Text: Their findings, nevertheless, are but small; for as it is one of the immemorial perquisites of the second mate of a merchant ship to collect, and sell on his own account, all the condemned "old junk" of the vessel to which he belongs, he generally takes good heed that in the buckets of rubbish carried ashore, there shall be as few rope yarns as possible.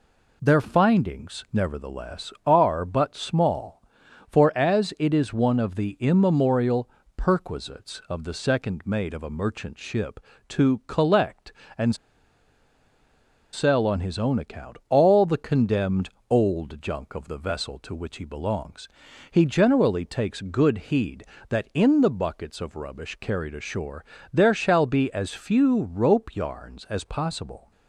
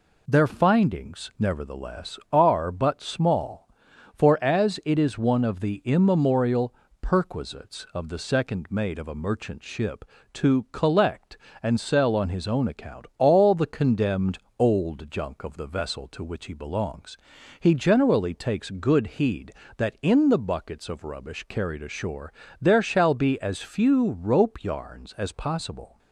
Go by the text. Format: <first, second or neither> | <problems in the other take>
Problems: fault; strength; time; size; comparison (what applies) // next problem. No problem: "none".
second | pauses between "immemorial" and "perquisites"; slight; at 6.8 s; 0.26 s long; slight in the second // pauses between "and" and "sell"; strong; at 11.9 s; 1.5 s long // pauses between "condemned" and "old"; slight; at 16.1 s; 0.18 s long; slight in the second